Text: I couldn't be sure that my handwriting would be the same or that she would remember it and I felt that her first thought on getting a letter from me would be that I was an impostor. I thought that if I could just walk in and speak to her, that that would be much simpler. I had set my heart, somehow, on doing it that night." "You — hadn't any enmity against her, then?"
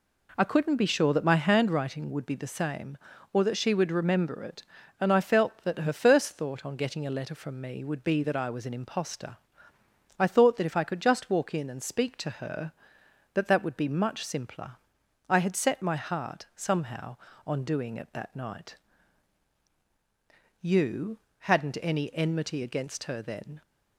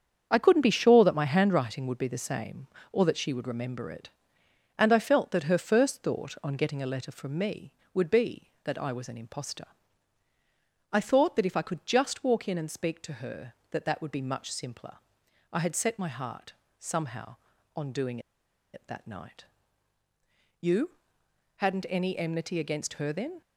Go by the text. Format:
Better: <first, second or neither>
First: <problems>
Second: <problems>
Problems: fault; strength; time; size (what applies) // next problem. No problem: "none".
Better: first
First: none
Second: starts louder than the rest; strong; until 1.3 s; 7.5 dB // pauses between "doing" and "it"; noticeable; at 18.1 s; 0.54 s long